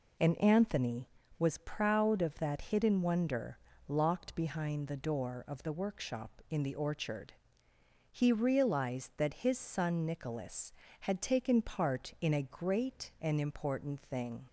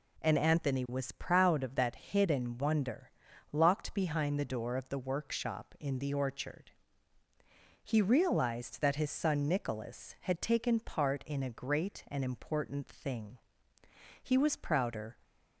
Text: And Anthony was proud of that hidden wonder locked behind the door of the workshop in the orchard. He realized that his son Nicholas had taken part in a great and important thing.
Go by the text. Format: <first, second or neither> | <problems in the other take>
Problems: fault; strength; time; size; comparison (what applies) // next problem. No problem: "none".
first | pauses between "wonder" and "locked"; at 3.0 s; 0.42 s long; slight in the first // goes on to say "He was prouder"; noticeable; from 14.2 s on; 0.94 s long